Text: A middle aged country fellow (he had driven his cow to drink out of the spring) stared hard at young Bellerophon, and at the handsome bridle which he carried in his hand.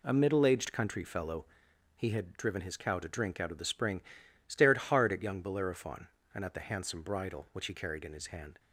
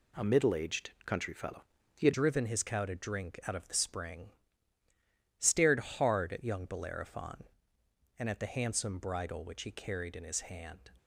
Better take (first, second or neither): first